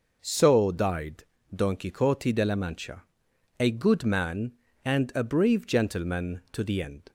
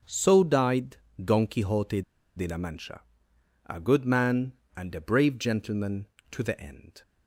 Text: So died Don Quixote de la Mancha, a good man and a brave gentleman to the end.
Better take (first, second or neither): first